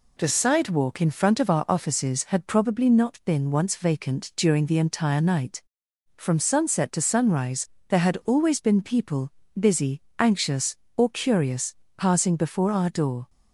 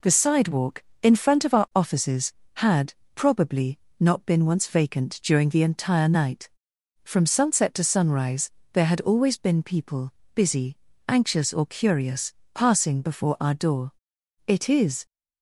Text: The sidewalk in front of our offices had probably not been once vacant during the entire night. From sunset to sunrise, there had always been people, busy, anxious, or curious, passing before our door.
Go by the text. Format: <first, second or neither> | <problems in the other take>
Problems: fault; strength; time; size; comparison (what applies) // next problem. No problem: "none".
first | pauses between "had" and "probably"; slight; at 2.9 s; 0.18 s long // pauses between "probably" and "not"; slight; at 3.7 s; 0.22 s long // goes on to say "It is"; from 14.4 s on; 0.58 s long